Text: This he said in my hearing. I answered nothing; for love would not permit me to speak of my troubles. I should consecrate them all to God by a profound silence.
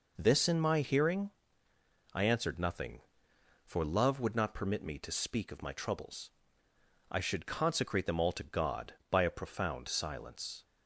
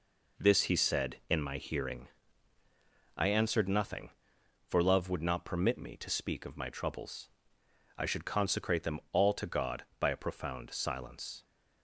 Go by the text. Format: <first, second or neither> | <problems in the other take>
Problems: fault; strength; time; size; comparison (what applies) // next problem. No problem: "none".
second | skips "he said"; at 0.4 s